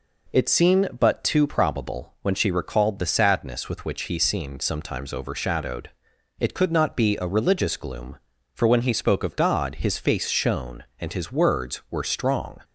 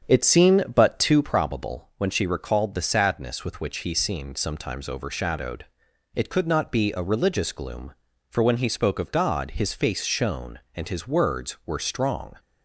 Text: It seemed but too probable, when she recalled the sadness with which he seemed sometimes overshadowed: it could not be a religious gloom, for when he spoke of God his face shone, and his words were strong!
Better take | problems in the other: first | starts louder than the rest; strong; until 1.4 s; 8 dB

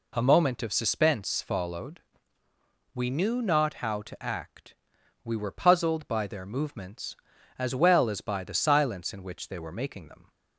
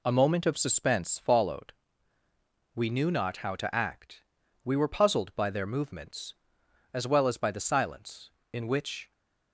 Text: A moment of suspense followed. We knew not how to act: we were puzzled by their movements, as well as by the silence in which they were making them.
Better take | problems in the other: first | stops before "they were making them"; at 9.1 s

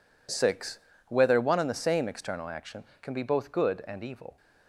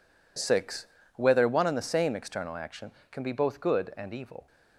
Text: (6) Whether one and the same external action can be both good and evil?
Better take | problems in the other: neither | none

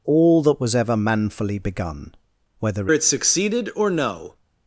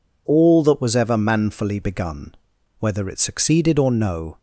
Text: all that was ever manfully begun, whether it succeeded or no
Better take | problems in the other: second | changes voice at "it"; from 2.9 s on; 1.4 s long

